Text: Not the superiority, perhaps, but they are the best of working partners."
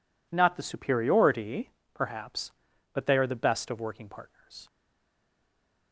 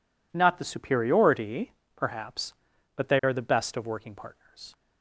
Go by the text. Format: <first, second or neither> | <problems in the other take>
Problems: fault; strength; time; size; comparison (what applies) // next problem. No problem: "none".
second | stays silent after the last word; noticeable; from 4.6 s on; 1.3 s long